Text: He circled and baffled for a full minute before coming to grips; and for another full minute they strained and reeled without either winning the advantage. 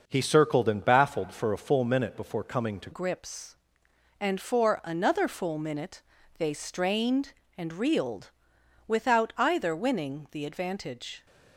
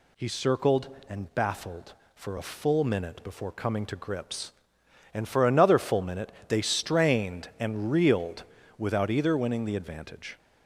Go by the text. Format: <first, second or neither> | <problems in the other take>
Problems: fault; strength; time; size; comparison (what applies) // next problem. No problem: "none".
second | changes voice at "grips"; from 2.9 s on; 8.3 s long // pauses between "minute" and "they"; slight; at 6.0 s; 0.36 s long; slight in the second // pauses between "reeled" and "without"; noticeable; at 8.2 s; 0.58 s long; slight in the second